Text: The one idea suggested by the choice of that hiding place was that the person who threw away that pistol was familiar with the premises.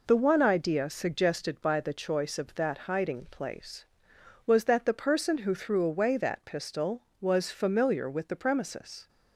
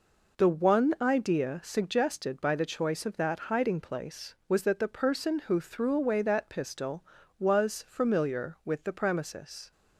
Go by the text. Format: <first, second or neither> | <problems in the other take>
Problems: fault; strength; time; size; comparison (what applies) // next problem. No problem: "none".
neither | none